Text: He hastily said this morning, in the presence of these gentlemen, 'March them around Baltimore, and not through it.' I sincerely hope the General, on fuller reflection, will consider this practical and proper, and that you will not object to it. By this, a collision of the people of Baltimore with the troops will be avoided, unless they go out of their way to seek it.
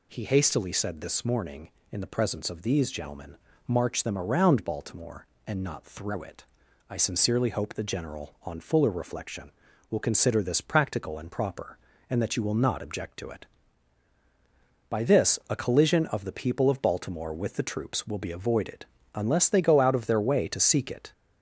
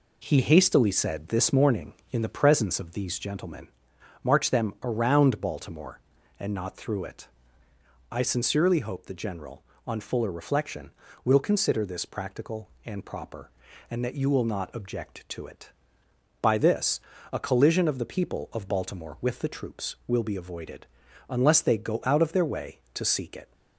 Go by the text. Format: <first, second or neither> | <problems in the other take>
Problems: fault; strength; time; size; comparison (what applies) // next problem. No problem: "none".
second | gets louder; slight; throughout; 2.5 dB